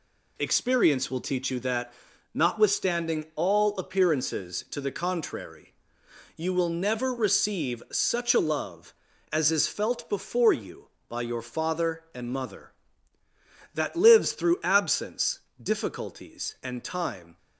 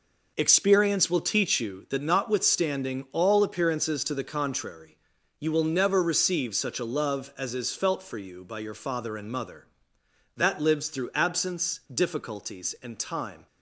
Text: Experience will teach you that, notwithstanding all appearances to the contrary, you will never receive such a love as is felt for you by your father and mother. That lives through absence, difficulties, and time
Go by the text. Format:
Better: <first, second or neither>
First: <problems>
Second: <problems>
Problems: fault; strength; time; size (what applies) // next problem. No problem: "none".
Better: second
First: says "before" for "for"; at 10.0 s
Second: none